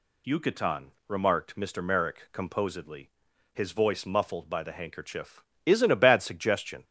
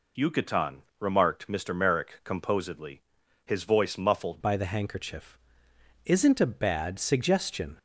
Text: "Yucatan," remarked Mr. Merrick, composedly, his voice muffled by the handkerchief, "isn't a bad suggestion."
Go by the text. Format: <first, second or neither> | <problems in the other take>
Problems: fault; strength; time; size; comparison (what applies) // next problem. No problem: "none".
first | changes voice at "by"; from 4.4 s on; 3.3 s long